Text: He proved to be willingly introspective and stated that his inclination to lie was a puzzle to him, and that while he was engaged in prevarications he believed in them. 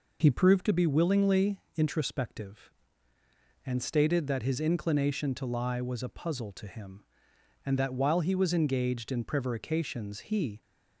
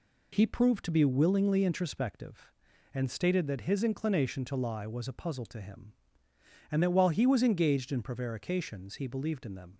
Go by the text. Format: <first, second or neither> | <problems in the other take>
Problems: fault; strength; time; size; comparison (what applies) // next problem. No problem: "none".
second | pauses between "willingly" and "introspective"; slight; at 1.5 s; 0.18 s long // stops before "believed in them"; at 10.6 s